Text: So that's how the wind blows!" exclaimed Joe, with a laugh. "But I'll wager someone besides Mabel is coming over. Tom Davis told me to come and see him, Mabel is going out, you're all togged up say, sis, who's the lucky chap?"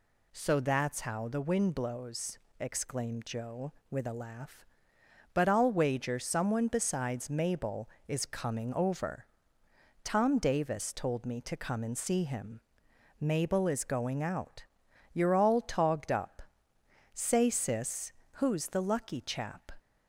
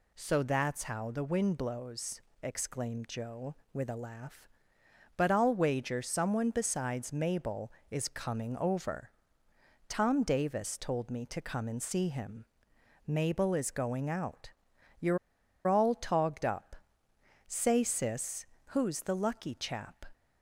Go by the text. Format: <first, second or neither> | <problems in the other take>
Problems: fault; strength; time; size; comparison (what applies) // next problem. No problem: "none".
first | pauses between "you're" and "all"; noticeable; at 15.1 s; 0.49 s long // pauses between "up" and "say"; noticeable; at 16.7 s; 0.72 s long; noticeable in the first